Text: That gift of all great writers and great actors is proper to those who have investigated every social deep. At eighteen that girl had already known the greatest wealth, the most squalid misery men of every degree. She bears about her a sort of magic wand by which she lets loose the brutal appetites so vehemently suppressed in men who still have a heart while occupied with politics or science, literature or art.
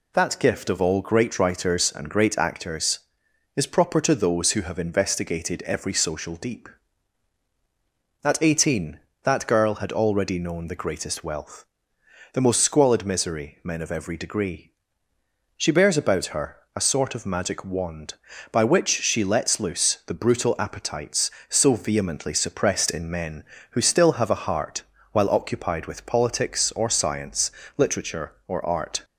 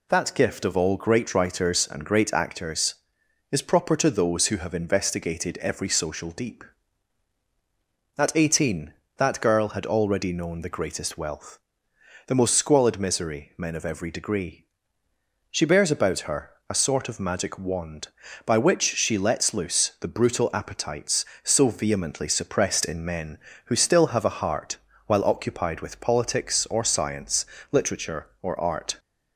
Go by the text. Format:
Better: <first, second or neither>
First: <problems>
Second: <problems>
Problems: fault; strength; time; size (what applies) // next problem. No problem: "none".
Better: neither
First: pauses between "her" and "a"; slight; at 16.5 s; 0.18 s long // pauses between "heart" and "while"; slight; at 24.8 s; 0.30 s long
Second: pauses between "her" and "a"; slight; at 16.4 s; 0.18 s long // pauses between "heart" and "while"; slight; at 24.7 s; 0.30 s long